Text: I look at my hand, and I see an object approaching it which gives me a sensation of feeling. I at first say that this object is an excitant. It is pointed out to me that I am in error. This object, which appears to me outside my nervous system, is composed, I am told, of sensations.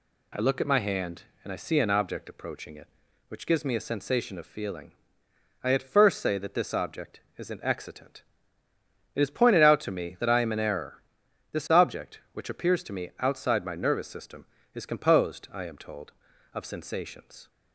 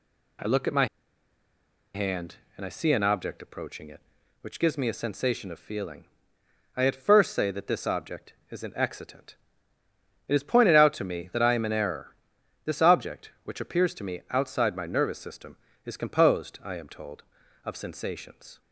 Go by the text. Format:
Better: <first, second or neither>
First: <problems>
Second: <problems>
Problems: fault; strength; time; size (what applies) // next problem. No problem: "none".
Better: first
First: none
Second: pauses between "my" and "hand"; at 0.8 s; 1.0 s long